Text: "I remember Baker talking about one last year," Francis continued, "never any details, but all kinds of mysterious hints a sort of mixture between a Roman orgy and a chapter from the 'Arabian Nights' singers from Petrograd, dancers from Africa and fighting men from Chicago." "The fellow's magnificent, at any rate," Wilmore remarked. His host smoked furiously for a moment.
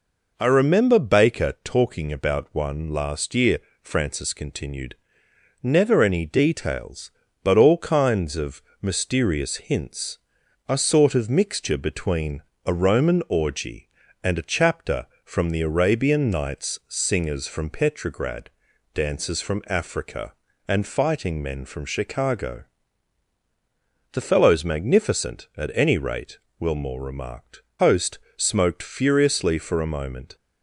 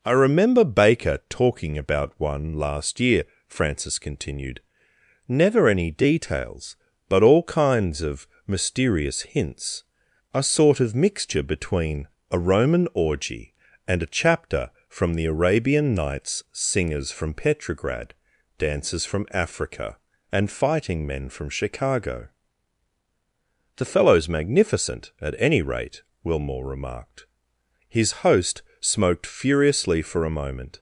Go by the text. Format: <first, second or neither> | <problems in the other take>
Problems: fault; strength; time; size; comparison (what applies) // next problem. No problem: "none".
second | pauses between "of" and "mysterious"; slight; at 8.6 s; 0.20 s long; slight in the second // pauses between "hints" and "a"; noticeable; at 10.1 s; 0.48 s long; noticeable in the second // pauses between "between" and "a"; slight; at 12.4 s; 0.24 s long; slight in the second // skips "His"; at 27.7 s // pauses between "host" and "smoked"; slight; at 28.1 s; 0.20 s long; slight in the second